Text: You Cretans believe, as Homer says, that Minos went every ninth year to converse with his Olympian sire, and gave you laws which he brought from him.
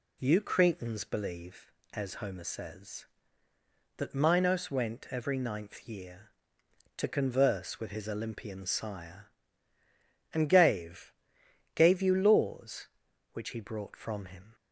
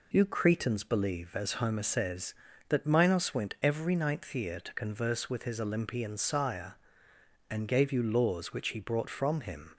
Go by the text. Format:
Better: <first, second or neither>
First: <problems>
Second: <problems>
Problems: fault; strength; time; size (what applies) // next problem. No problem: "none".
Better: second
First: says "gave" twice; at 11.7 s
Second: none